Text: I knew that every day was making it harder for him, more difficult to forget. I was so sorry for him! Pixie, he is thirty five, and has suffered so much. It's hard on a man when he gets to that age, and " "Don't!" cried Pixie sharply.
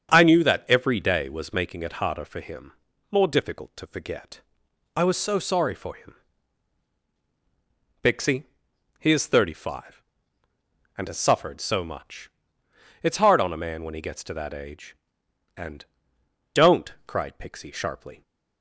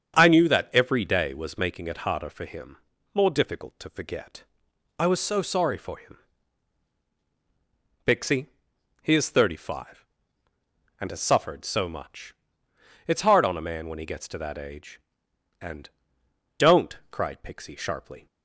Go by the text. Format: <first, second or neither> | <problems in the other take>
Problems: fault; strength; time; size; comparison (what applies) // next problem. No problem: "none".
neither | starts louder than the rest; strong; the same in both